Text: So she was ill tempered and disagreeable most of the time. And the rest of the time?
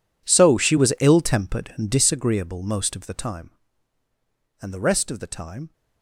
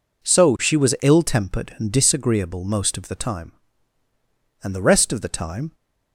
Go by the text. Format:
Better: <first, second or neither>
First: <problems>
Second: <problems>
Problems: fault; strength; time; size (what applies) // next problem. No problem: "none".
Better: second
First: gets quieter; strong; throughout; 20 dB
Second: none